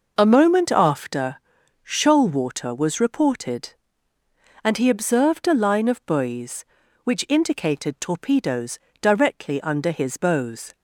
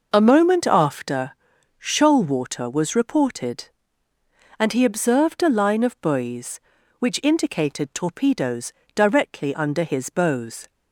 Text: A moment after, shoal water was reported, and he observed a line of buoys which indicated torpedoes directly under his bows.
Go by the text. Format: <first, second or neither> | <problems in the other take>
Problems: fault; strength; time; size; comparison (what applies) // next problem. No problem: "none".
neither | pauses between "torpedoes" and "directly"; slight; the same in both